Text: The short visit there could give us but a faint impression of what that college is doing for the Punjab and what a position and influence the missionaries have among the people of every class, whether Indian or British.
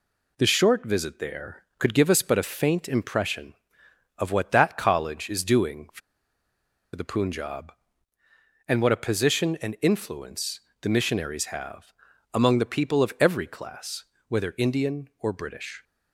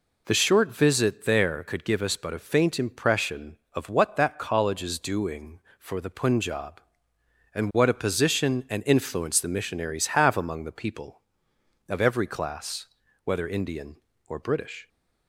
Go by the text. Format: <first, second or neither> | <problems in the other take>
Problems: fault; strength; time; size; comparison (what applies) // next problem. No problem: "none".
second | pauses between "for" and "the"; noticeable; at 6.0 s; 0.94 s long // pauses between "influence" and "the"; slight; at 10.6 s; 0.22 s long // pauses between "have" and "among"; at 11.9 s; 0.42 s long